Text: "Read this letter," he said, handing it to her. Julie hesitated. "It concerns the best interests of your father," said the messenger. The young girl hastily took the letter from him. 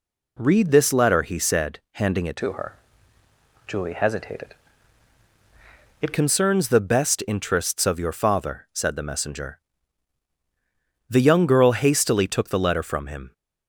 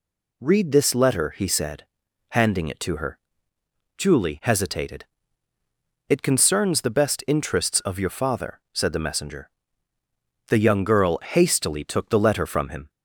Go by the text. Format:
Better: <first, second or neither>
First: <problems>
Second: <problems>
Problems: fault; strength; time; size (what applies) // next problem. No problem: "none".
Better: second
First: changes voice from "to" to "It"; from 2.3 to 6.1 s; 3.8 s long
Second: none